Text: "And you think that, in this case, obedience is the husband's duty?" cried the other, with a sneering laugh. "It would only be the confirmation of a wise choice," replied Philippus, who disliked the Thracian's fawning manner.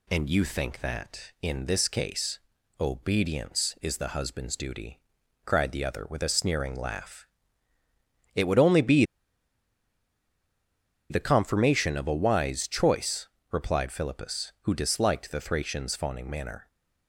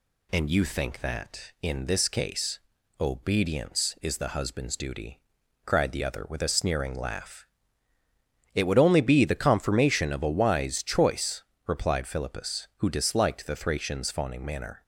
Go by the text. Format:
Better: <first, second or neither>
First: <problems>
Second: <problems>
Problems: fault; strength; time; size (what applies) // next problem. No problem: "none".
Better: second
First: pauses between "be" and "the"; strong; at 9.0 s; 2.0 s long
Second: none